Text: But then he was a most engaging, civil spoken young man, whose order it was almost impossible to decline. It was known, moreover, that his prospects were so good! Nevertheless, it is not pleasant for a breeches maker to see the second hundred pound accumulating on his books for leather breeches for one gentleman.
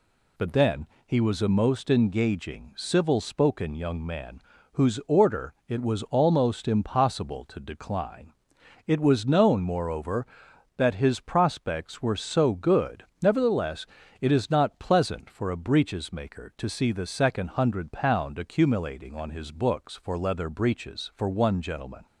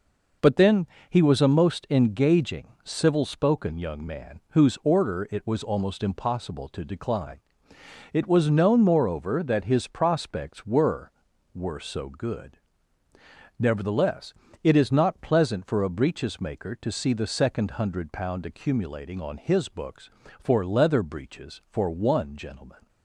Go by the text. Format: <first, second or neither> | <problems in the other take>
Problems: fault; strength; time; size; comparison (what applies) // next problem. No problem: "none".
first | pauses between "then" and "he"; slight; at 0.8 s; 0.22 s long; slight in the first // says "were" twice; at 11.5 s